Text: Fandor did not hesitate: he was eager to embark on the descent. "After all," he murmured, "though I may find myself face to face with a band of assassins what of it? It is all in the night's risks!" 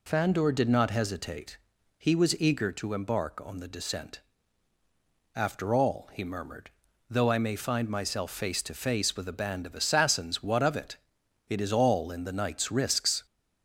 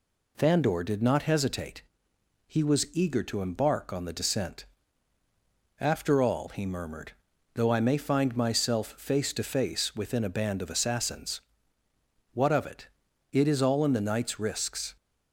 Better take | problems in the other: first | says "within" for "with"; at 9.9 s // pauses between "assassins" and "what"; noticeable; at 11.3 s; 0.94 s long

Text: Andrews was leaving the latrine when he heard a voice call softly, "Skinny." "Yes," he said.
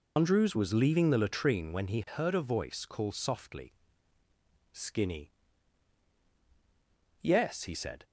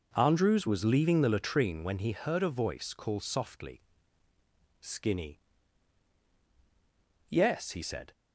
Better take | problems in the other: second | loses the start of "Andrews"; at 0.1 s; 150 ms

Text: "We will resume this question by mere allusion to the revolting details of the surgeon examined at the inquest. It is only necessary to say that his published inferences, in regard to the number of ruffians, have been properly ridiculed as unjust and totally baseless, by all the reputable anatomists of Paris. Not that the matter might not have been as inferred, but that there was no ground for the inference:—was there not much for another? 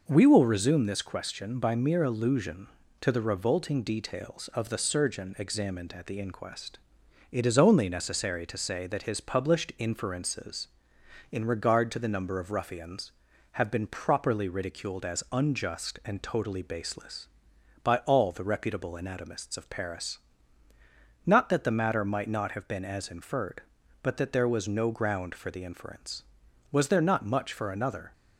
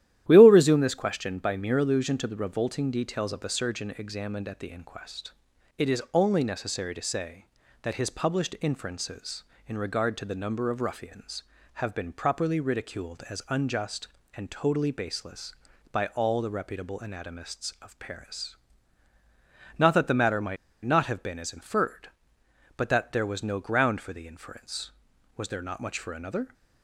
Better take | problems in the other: first | starts louder than the rest; strong; until 1.2 s; 12.5 dB // pauses between "might" and "not"; slight; at 20.5 s; 0.28 s long

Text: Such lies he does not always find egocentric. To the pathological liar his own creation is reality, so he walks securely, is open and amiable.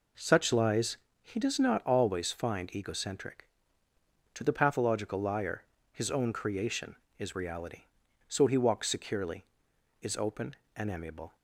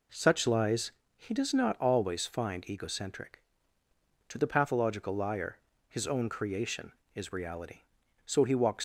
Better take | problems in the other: first | pauses between "lies" and "he"; slight; at 0.9 s; 0.26 s long; slight in the first // pauses between "liar" and "his"; slight; at 5.5 s; 0.29 s long; slight in the first // stops before "securely is open and amiable"; at 8.7 s

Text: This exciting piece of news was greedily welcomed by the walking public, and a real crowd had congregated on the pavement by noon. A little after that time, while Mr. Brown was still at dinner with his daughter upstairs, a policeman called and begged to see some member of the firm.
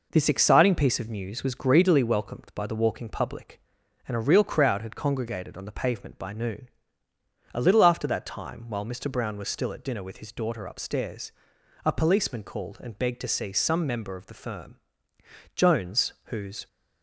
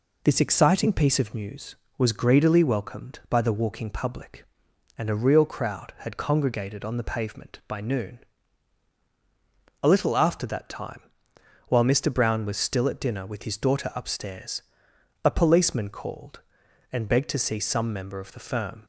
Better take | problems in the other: second | goes on to say "Jones whose"; noticeable; from 15.5 s on; 1.1 s long

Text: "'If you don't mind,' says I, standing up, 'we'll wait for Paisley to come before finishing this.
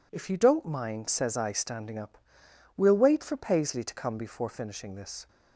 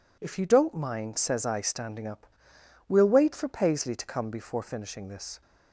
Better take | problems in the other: neither | none

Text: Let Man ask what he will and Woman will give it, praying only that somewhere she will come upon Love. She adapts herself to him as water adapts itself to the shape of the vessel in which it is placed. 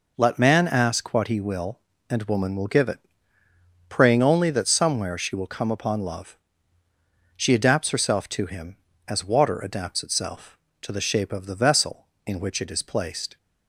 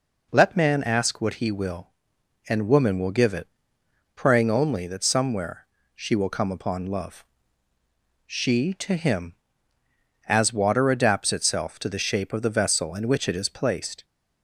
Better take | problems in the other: first | pauses between "somewhere" and "she"; slight; at 5.6 s; 0.28 s long // skips "adapts herself"; at 8.7 s

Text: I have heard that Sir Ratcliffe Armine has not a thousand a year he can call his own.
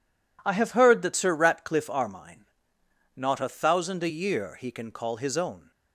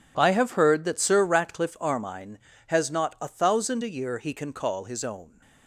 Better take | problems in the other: second | skips "has"; at 2.7 s

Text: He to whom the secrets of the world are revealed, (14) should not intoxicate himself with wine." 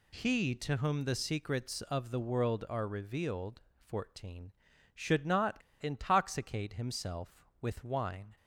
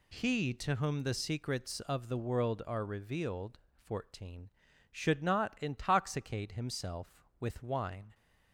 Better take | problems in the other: second | pauses between "not" and "intoxicate"; slight; at 5.5 s; 0.24 s long

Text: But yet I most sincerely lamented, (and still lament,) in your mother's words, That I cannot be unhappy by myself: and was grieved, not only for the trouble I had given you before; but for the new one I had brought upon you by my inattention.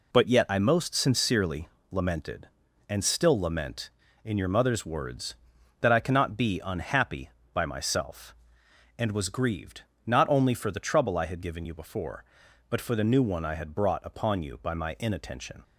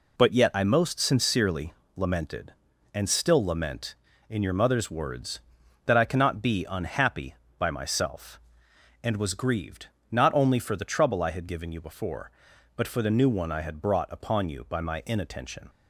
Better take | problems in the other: neither | pauses between "sincerely" and "lamented"; slight; the same in both

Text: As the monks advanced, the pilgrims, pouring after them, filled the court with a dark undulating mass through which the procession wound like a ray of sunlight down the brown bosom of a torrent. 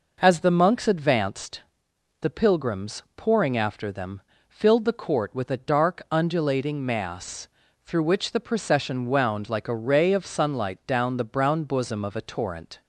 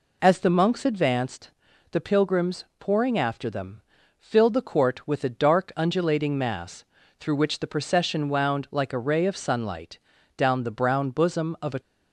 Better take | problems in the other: first | pauses between "mass" and "through"; slight; at 6.8 s; 0.36 s long; also in the first // pauses between "sunlight" and "down"; at 9.9 s; 0.38 s long // stops before "torrent"; at 11.7 s

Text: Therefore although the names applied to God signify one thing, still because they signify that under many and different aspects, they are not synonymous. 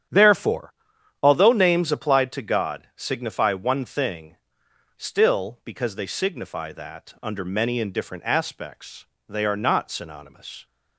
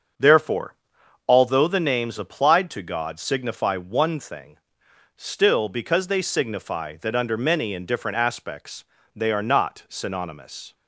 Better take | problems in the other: second | starts louder than the rest; strong; until 1.6 s; 9 dB; also in the second // pauses between "Therefore" and "although"; noticeable; at 0.7 s; 0.50 s long; noticeable in the second // skips "the"; at 1.5 s

